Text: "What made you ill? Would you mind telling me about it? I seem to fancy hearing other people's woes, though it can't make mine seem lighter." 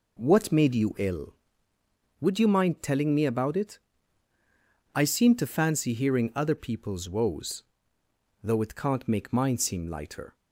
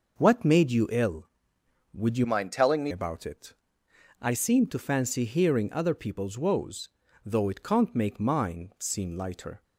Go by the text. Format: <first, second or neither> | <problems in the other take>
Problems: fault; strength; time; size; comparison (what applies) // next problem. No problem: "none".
first | changes voice from "mind" to "me"; from 2.2 to 2.9 s; 0.7 s long